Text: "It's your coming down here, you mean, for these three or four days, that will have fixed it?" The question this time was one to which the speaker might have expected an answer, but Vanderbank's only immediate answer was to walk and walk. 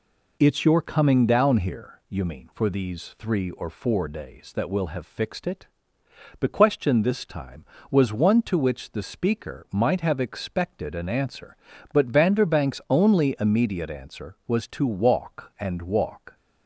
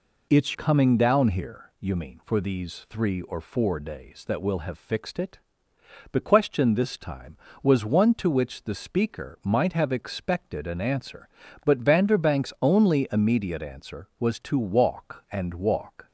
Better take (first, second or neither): first